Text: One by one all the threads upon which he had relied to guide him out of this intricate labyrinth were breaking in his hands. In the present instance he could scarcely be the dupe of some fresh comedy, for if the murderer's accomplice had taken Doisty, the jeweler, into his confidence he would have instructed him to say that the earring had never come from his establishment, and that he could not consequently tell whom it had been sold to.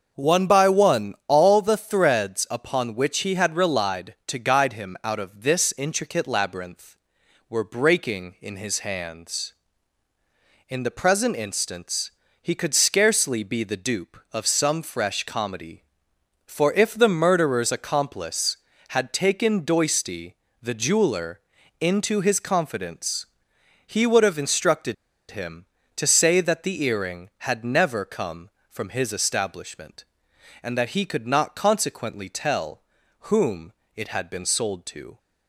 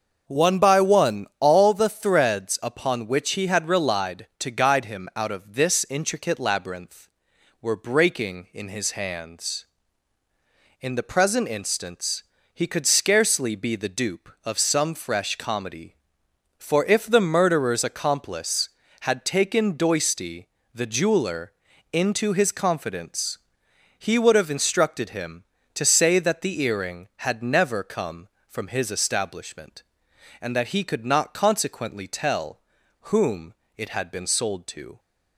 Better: second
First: starts louder than the rest; noticeable; until 1.1 s; 6 dB // pauses between "instance" and "he"; slight; at 12.1 s; 0.28 s long // pauses between "confidence" and "he"; noticeable; at 23.2 s; 0.58 s long // pauses between "instructed" and "him"; at 24.9 s; 0.36 s long // pauses between "tell" and "whom"; at 32.8 s; 0.40 s long // pauses between "whom" and "it"; slight; at 33.7 s; 0.22 s long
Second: starts louder than the rest; noticeable; until 1.2 s; 6 dB // pauses between "instance" and "he"; slight; at 12.2 s; 0.28 s long // pauses between "confidence" and "he"; noticeable; at 23.3 s; 0.58 s long // pauses between "tell" and "whom"; at 32.5 s; 0.42 s long // pauses between "whom" and "it"; slight; at 33.5 s; 0.22 s long

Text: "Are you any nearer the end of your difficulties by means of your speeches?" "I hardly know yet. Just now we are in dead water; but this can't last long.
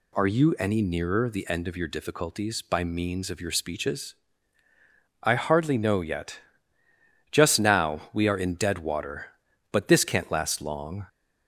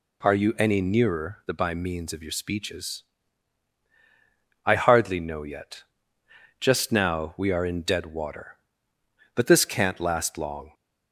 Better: first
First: none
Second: skips "end of your difficulties"; at 1.5 s

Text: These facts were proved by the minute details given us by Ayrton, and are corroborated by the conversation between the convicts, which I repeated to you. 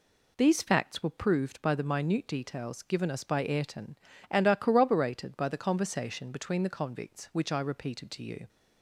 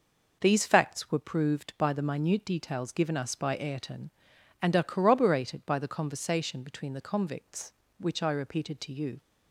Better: neither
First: none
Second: none

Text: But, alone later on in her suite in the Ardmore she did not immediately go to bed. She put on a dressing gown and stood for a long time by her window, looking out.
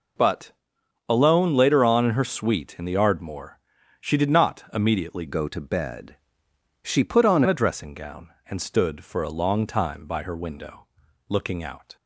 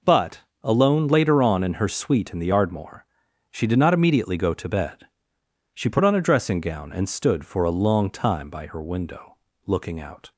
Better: second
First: pauses between "Ardmore" and "she"; at 3.5 s; 0.40 s long // changes voice from "go" to "on"; from 5.2 to 7.4 s; 2.2 s long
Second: pauses between "Ardmore" and "she"; noticeable; at 3.0 s; 0.46 s long

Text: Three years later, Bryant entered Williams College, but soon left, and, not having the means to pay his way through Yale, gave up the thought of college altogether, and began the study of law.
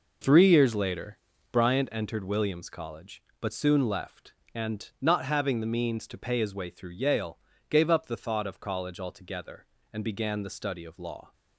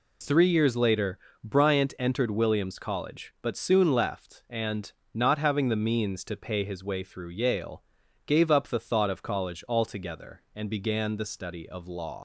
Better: first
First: none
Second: leaves "law" unfinished; at 12.1 s; 105 ms

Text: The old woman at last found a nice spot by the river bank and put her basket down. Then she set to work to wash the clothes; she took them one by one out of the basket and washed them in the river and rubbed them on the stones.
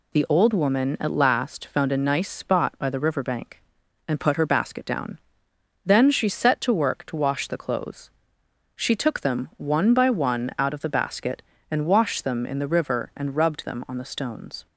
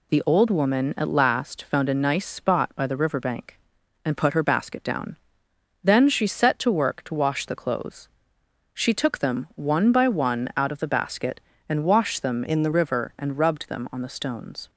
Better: first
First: none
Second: changes voice from "in" to "the"; from 12.4 to 12.7 s; 0.3 s long

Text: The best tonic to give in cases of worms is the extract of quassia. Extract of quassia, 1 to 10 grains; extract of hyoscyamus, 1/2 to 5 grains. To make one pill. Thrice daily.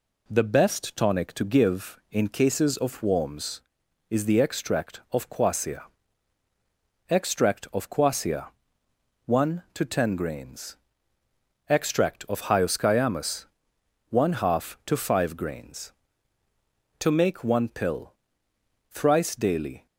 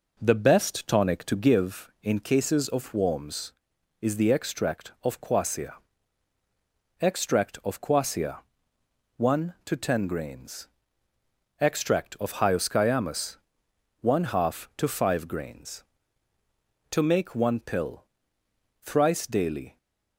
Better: first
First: none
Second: starts louder than the rest; noticeable; until 1.6 s; 4.5 dB

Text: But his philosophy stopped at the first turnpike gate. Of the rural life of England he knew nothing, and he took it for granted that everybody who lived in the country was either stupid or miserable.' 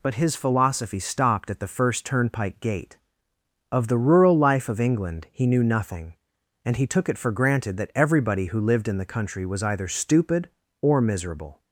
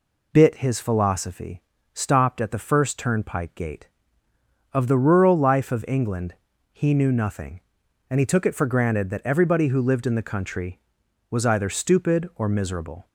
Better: first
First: none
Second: says "Bit" for "But"; at 0.3 s // pauses between "philosophy" and "stopped"; slight; at 1.6 s; 0.32 s long // pauses between "England" and "he"; at 6.3 s; 0.38 s long

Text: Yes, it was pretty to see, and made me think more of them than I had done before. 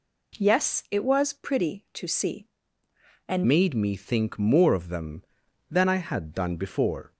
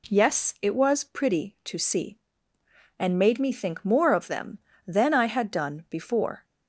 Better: second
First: changes voice at "made"; from 3.4 s on; 3.7 s long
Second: none

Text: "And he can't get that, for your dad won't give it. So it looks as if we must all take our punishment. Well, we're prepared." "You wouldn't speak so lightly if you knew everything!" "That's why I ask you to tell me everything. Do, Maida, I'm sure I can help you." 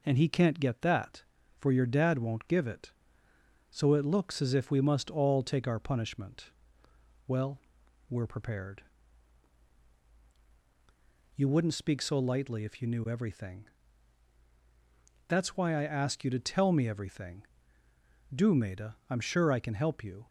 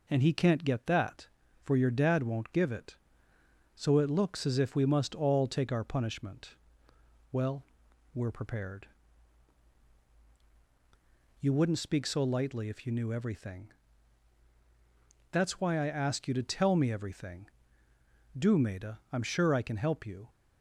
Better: neither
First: none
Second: none

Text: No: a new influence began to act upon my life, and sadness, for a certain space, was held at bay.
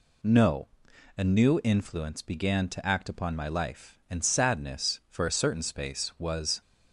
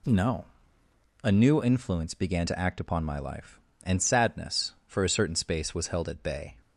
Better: second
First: stops before "held at bay"; at 6.5 s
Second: none

